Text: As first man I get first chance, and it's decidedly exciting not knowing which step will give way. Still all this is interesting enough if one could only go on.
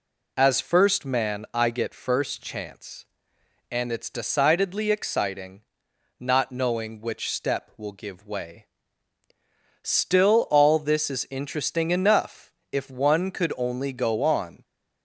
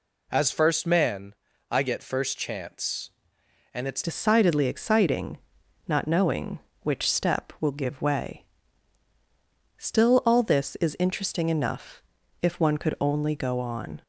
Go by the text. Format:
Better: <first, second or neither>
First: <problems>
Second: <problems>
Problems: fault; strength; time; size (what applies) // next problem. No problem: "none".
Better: first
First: pauses between "exciting" and "not"; noticeable; at 5.6 s; 0.58 s long // pauses between "enough" and "if"; slight; at 12.5 s; 0.18 s long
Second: pauses between "man" and "I"; slight; at 1.3 s; 0.36 s long // changes voice at "decidedly"; from 4.0 s on; 10.0 s long // pauses between "exciting" and "not"; noticeable; at 5.3 s; 0.50 s long // pauses between "enough" and "if"; at 12.0 s; 0.42 s long